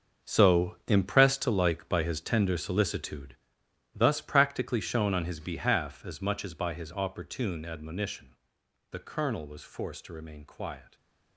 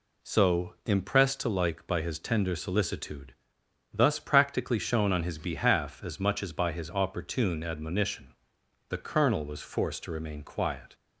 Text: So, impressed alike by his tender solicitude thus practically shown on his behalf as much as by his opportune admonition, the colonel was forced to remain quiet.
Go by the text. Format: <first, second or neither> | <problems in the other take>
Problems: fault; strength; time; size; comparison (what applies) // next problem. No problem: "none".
second | gets quieter; strong; throughout; 13 dB // pauses between "solicitude" and "thus"; noticeable; at 3.3 s; 0.58 s long; noticeable in the second